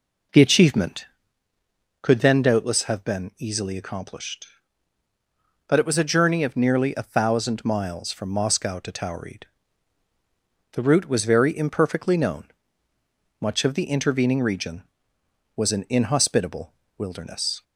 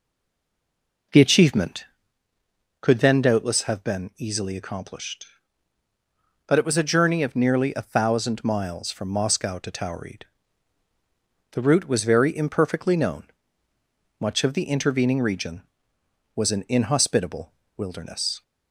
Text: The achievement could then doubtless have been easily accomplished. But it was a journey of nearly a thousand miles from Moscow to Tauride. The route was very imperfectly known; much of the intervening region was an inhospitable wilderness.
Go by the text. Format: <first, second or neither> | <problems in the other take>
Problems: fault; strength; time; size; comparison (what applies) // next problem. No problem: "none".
first | stays silent before the first word; until 1.1 s; 1.1 s long // pauses between "inhospitable" and "wilderness"; slight; at 17.5 s; 0.24 s long; slight in the first